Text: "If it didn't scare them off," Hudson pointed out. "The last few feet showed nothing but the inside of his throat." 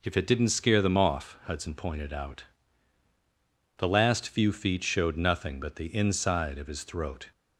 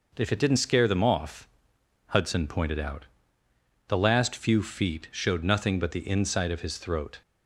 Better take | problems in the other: neither | none

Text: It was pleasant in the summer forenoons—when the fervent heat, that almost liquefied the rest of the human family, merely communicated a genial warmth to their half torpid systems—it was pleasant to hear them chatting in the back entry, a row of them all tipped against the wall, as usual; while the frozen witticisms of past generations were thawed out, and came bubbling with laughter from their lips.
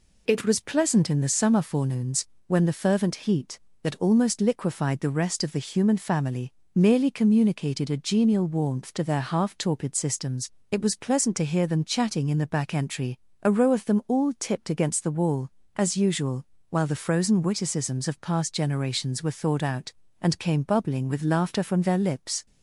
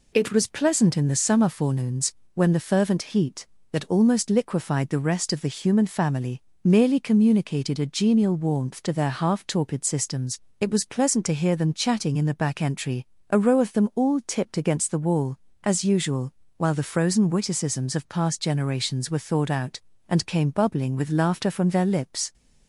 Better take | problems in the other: neither | none

